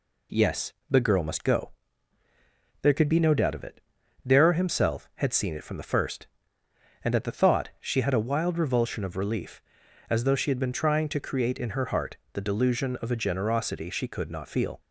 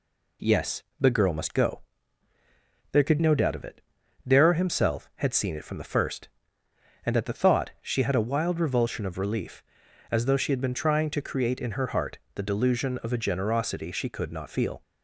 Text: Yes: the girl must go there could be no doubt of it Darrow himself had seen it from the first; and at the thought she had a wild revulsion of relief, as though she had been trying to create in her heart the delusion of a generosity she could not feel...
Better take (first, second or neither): first